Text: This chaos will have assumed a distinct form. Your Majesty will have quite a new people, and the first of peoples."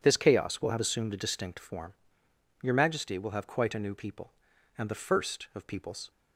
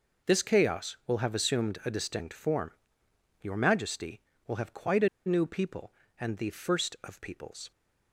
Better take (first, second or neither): first